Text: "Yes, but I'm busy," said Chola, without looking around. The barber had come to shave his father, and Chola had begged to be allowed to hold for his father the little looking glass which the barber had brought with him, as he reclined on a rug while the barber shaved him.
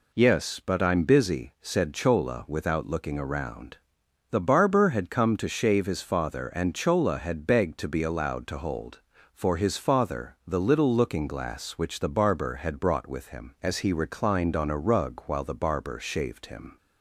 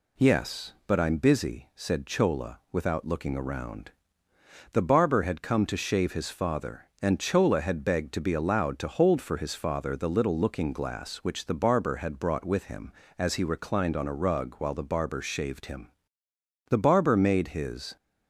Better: first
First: none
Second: goes on to say "The barber made his"; noticeable; from 16.6 s on; 1.2 s long

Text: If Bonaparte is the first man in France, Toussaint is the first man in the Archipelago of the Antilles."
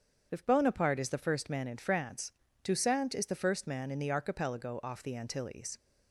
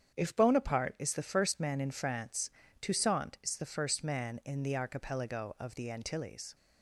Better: second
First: starts louder than the rest; strong; until 1.3 s; 7.5 dB // says "off" for "of"; at 4.8 s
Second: starts louder than the rest; strong; until 1.1 s; 8.5 dB

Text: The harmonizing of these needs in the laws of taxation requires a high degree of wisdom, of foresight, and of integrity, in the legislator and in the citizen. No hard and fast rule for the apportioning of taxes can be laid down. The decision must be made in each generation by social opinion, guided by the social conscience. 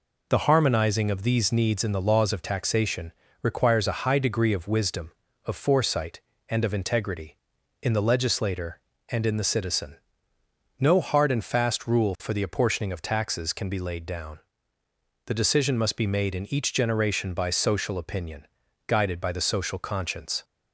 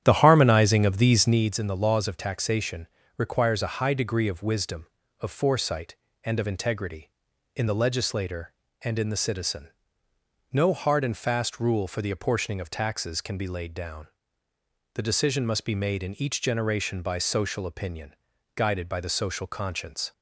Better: first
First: pauses between "taxation" and "requires"; slight; at 3.1 s; 0.28 s long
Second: starts louder than the rest; strong; until 1.5 s; 10 dB // pauses between "taxation" and "requires"; slight; at 2.8 s; 0.28 s long

